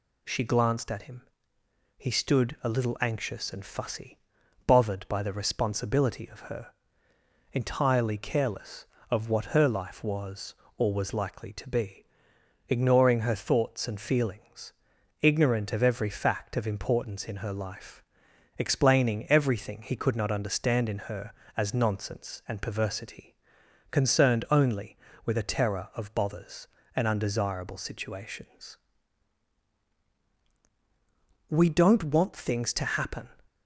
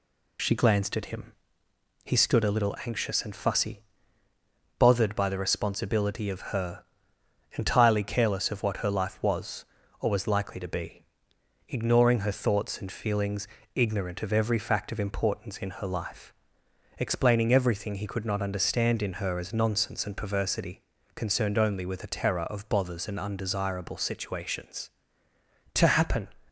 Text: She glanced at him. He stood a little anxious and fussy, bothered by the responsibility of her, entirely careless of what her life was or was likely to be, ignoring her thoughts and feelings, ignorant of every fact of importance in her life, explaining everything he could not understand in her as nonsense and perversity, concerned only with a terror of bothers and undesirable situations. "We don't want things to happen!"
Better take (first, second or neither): first